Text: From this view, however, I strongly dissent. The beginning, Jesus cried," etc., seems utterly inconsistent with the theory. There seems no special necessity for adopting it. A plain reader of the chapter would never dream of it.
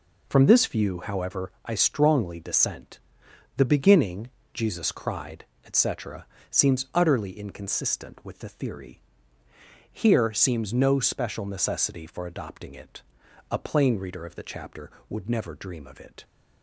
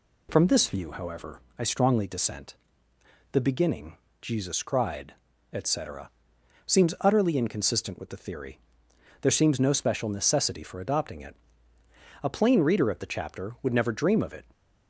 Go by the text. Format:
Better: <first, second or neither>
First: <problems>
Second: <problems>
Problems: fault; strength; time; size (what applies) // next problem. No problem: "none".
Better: second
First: says "Here" for "There"; at 9.9 s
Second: none